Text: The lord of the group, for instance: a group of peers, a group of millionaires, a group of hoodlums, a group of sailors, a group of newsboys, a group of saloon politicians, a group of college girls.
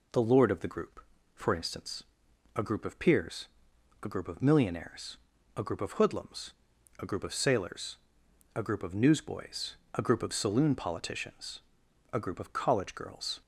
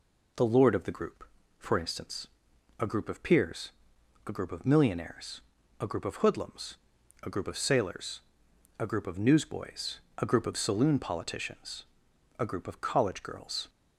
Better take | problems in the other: neither | none

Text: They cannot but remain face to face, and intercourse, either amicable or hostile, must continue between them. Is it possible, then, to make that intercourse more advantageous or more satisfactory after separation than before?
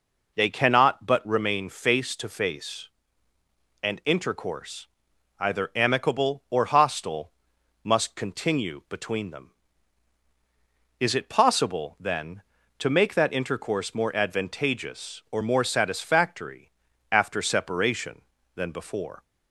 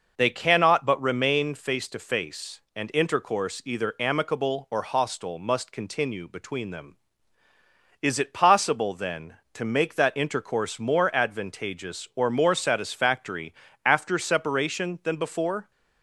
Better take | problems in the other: neither | pauses between "satisfactory" and "after"; the same in both

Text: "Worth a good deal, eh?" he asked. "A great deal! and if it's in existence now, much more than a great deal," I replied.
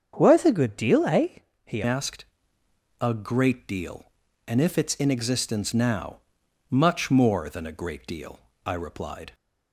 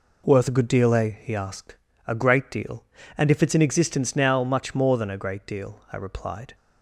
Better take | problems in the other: second | starts louder than the rest; strong; until 1.1 s; 7.5 dB // changes voice at "asked"; from 1.8 s on; 7.5 s long

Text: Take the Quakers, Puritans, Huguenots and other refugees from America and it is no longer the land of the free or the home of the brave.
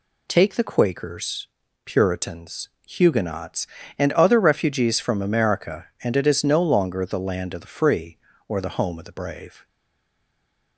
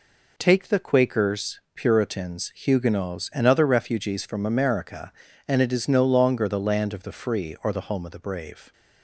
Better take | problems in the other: second | stays silent after the last word; from 9.6 s on; 1.1 s long

